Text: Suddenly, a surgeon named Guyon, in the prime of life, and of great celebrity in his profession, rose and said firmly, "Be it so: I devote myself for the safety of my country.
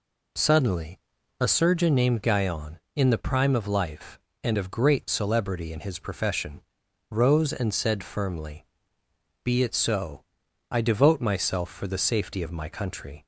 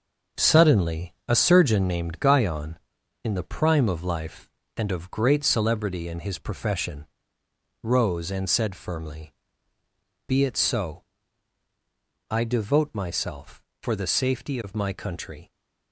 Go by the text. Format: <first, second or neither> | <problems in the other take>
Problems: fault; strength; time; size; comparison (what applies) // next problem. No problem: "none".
first | gets quieter; strong; throughout; 7.5 dB